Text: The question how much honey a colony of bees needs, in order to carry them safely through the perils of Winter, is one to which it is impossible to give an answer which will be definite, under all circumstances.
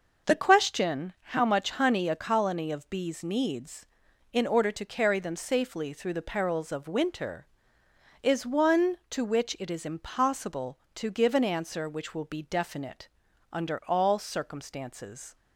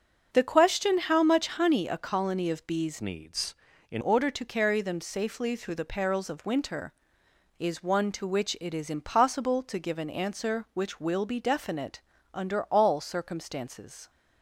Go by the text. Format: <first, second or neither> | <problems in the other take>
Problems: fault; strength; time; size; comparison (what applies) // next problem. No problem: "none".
first | starts louder than the rest; until 1.3 s; 6.5 dB // changes voice from "needs" to "in"; from 2.9 to 4.0 s; 1.1 s long